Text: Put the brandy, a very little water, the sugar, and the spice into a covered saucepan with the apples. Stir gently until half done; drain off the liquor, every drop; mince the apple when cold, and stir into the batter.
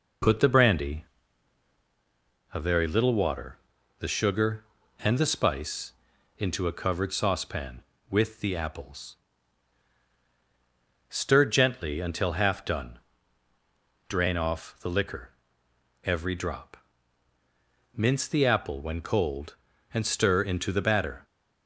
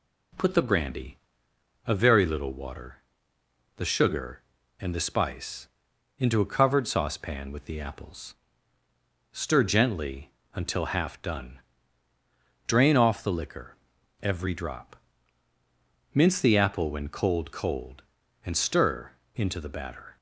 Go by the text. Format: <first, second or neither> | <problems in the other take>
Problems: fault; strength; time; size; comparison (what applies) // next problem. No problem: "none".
first | pauses between "spice" and "into"; noticeable; at 5.6 s; 0.50 s long; noticeable in the first // pauses between "gently" and "until"; slight; at 10.3 s; 0.22 s long // says "cold" twice; at 17.5 s // pauses between "stir" and "into"; slight; at 19.1 s; 0.24 s long